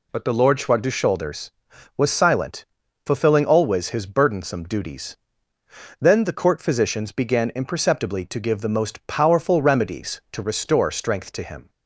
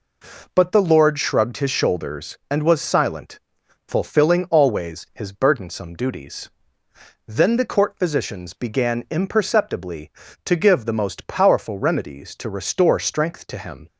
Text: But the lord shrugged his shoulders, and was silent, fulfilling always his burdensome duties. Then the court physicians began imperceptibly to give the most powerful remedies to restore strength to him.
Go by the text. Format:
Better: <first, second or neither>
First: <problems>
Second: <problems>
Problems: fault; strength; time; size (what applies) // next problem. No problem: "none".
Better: second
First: skips "and"; at 1.7 s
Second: none